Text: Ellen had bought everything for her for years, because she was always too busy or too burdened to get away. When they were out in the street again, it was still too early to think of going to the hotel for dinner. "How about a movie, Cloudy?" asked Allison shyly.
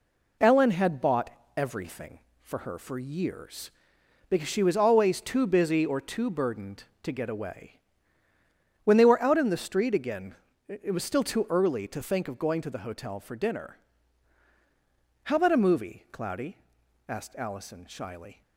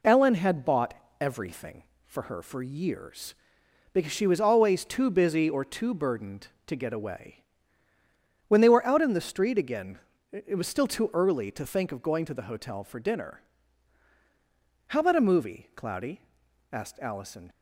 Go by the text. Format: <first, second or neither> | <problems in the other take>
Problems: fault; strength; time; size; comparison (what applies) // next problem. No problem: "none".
first | pauses between "bought" and "everything"; slight; at 0.9 s; 0.26 s long; slight in the first // stops before "shyly"; at 17.5 s